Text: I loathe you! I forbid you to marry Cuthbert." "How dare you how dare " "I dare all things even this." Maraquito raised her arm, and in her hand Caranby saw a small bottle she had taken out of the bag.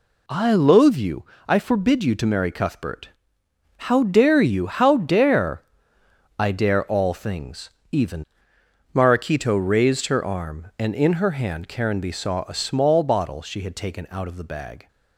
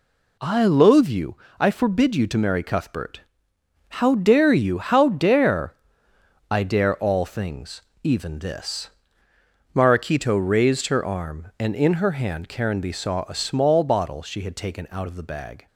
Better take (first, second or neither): second